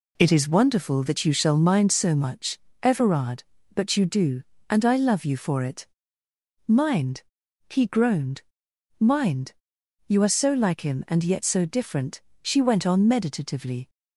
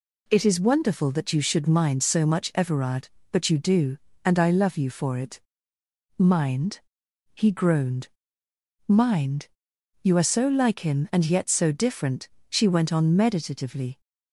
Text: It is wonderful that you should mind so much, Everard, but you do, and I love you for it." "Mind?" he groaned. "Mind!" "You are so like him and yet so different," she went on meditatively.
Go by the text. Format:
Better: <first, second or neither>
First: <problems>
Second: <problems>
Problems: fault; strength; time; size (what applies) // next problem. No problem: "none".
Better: second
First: says "shall" for "should"; at 1.3 s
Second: none